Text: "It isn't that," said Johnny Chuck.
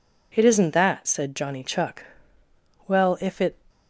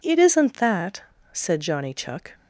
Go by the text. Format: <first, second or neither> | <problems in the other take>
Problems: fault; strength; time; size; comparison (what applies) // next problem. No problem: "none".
second | goes on to say "Well if it"; noticeable; from 2.8 s on; 0.68 s long